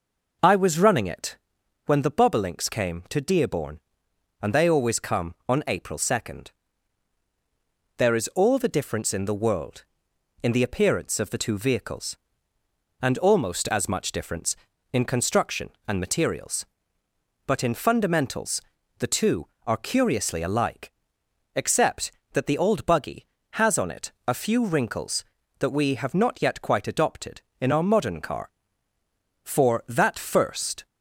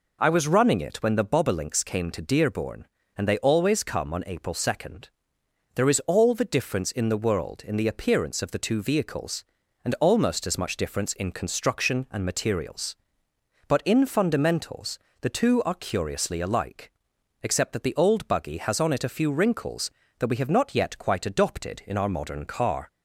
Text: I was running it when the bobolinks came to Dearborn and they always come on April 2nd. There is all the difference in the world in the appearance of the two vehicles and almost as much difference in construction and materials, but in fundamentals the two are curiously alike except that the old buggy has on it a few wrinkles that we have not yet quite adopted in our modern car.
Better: second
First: pauses between "it" and "when"; noticeable; at 1.3 s; 0.48 s long // pauses between "fundamentals" and "the"; at 18.6 s; 0.38 s long // pauses between "alike" and "except"; noticeable; at 20.8 s; 0.64 s long // goes on to say "For that first"; from 29.4 s on; 1.4 s long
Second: pauses between "fundamentals" and "the"; slight; at 14.9 s; 0.22 s long // pauses between "alike" and "except"; noticeable; at 16.9 s; 0.50 s long

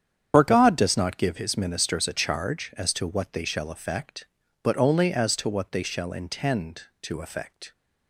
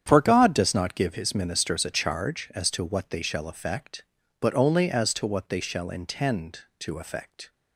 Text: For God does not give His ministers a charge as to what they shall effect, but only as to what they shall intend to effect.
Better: second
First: loses the start of "For"; at 0.3 s; 55 ms // starts louder than the rest; strong; until 1.3 s; 8.5 dB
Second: starts louder than the rest; strong; until 1.0 s; 9 dB

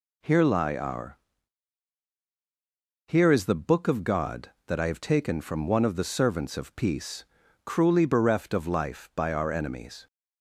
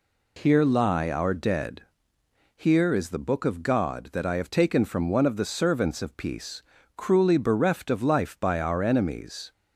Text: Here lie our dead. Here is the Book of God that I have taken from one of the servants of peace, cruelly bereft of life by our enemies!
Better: second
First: skips "dead"; at 2.1 s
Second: none

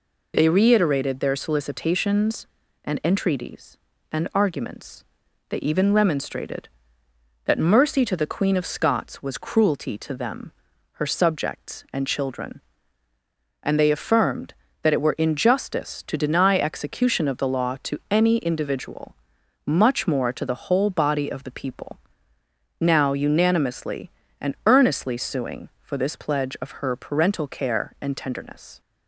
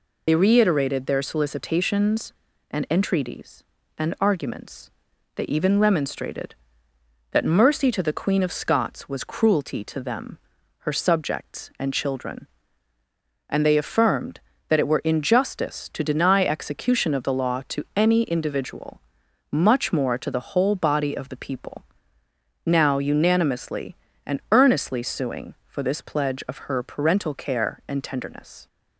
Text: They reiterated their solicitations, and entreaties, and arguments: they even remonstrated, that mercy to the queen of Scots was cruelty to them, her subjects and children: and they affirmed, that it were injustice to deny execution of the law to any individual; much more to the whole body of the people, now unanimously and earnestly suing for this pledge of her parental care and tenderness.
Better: first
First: none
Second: loses the start of "They"; at 0.2 s; 75 ms

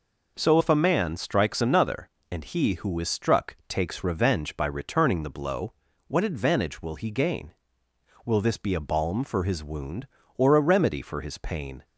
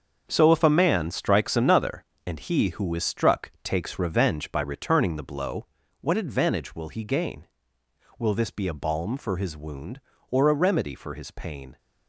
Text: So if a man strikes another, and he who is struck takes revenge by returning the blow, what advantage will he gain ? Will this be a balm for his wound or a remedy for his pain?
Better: first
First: none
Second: gets quieter; strong; throughout; 10 dB

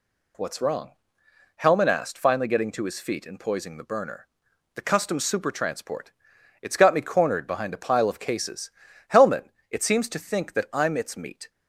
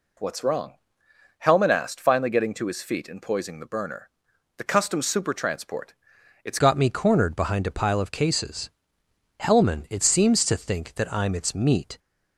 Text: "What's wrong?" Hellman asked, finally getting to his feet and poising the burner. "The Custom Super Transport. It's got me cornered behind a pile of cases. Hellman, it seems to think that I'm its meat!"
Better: first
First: none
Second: changes voice at "got"; from 6.5 s on; 5.4 s long

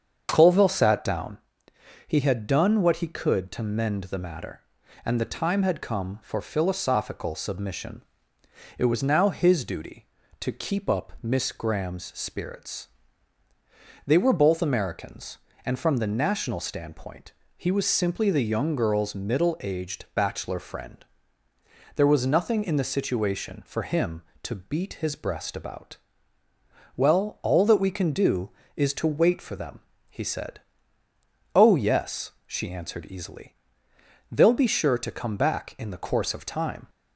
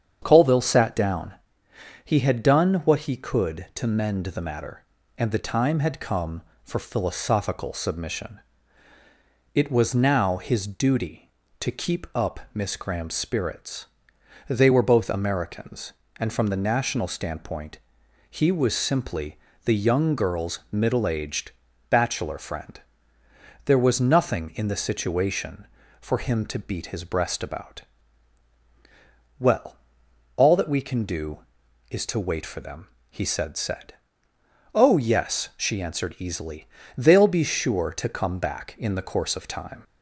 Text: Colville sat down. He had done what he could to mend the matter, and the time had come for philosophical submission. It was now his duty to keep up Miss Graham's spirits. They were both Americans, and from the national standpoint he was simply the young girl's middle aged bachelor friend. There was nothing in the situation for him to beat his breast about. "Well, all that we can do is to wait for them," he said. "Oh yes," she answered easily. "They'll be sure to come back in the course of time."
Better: first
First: starts louder than the rest; strong; until 1.3 s; 7 dB // pauses between "standpoint" and "he"; slight; at 17.3 s; 0.26 s long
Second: starts louder than the rest; strong; until 1.2 s; 8 dB // pauses between "standpoint" and "he"; noticeable; at 17.7 s; 0.52 s long // pauses between "simply" and "the"; slight; at 19.3 s; 0.28 s long // pauses between "aged" and "bachelor"; at 21.5 s; 0.38 s long // says "said" twice; at 33.5 s

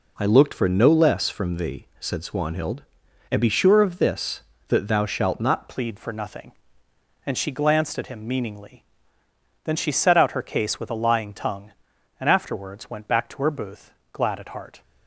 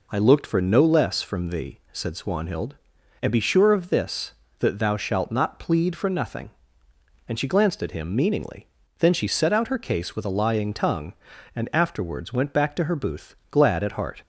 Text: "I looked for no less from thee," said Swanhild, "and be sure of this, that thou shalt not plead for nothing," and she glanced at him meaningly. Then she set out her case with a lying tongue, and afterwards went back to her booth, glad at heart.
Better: second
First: changes voice at "plead"; from 5.6 s on; 9.2 s long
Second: none

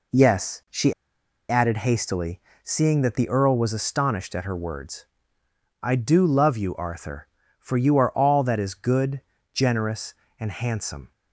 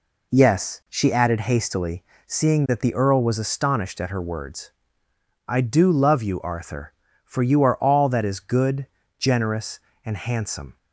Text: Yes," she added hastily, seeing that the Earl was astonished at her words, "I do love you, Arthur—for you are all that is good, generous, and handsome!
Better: second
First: pauses between "she" and "added"; noticeable; at 0.9 s; 0.57 s long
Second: none

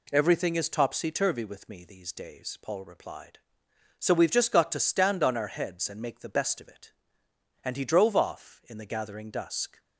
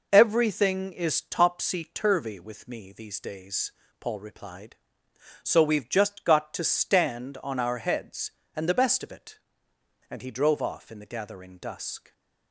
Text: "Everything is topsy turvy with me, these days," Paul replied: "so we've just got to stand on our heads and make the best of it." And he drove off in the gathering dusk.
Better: first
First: none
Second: skips "make"; at 8.6 s

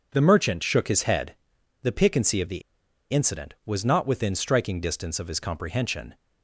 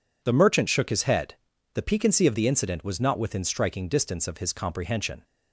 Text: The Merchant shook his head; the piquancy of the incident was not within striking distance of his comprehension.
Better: second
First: pauses between "the" and "incident"; noticeable; at 2.6 s; 0.50 s long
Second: none

